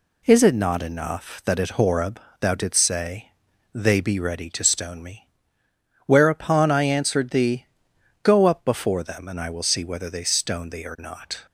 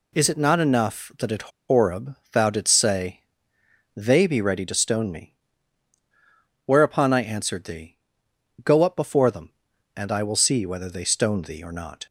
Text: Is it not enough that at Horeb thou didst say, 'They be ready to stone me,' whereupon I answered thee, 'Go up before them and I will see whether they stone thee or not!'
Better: first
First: pauses between "Horeb" and "thou"; slight; at 2.1 s; 0.22 s long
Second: pauses between "at" and "Horeb"; slight; at 1.4 s; 0.18 s long // pauses between "Horeb" and "thou"; slight; at 2.1 s; 0.16 s long

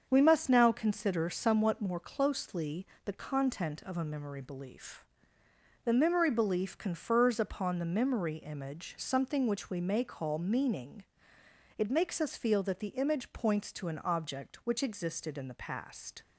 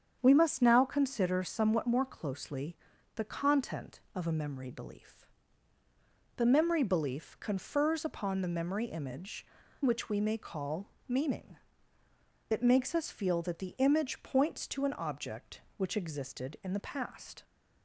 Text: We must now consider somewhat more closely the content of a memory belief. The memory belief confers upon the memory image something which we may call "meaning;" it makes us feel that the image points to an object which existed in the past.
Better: first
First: starts louder than the rest; until 1.1 s; 7 dB // pauses between "closely" and "the"; slight; at 2.8 s; 0.18 s long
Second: starts louder than the rest; strong; until 1.2 s; 8 dB // pauses between "closely" and "the"; at 2.7 s; 0.40 s long // skips "something"; at 9.6 s // pauses between "call" and "meaning"; slight; at 10.8 s; 0.18 s long

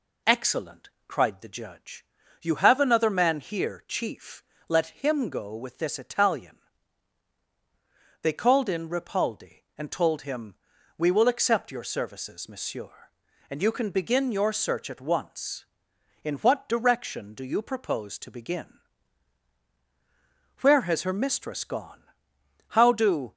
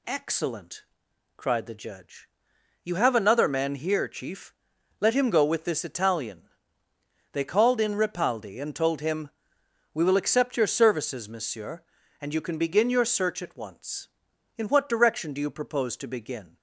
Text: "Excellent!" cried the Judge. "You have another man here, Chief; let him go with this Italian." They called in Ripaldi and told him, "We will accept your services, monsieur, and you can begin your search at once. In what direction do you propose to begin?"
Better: second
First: goes on to say "Where has her mistress gone How do"; strong; from 20.6 s on; 2.7 s long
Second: none

